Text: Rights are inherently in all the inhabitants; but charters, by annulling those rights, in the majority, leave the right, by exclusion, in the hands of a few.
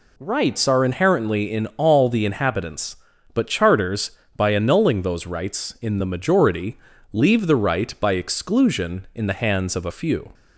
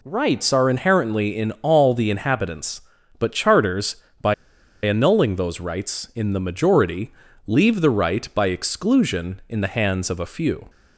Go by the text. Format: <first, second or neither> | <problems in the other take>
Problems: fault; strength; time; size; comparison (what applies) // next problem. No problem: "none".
first | pauses between "by" and "annulling"; noticeable; at 4.3 s; 0.51 s long